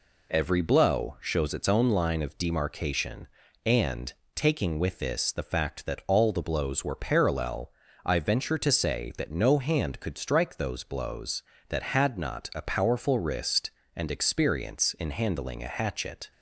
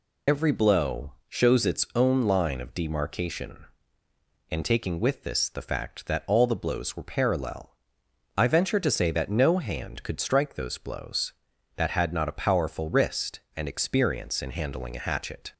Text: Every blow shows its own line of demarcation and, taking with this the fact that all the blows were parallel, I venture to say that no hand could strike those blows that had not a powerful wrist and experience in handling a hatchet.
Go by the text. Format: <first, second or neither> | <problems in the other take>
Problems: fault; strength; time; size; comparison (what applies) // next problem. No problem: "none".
first | loses the start of "Every"; at 0.2 s; 80 ms // pauses between "blow" and "shows"; slight; at 1.1 s; 0.16 s long